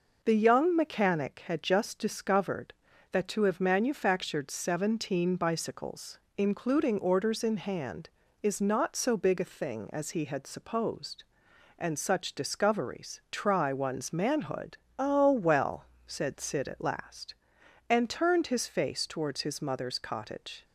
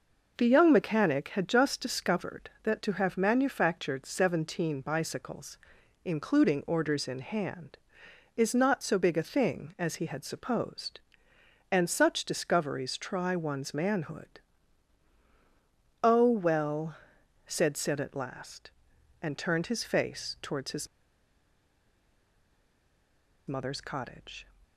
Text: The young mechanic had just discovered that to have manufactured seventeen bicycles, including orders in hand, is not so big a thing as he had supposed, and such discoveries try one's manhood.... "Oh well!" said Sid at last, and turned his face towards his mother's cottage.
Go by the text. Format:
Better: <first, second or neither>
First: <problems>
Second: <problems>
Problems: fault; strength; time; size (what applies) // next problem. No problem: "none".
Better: first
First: none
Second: pauses between "his" and "mother's"; strong; at 20.8 s; 2.6 s long